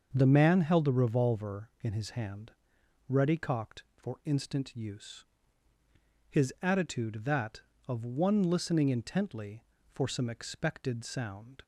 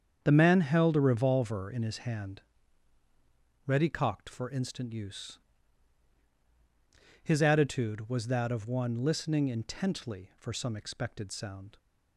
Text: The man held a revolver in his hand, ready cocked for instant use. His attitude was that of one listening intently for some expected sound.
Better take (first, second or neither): second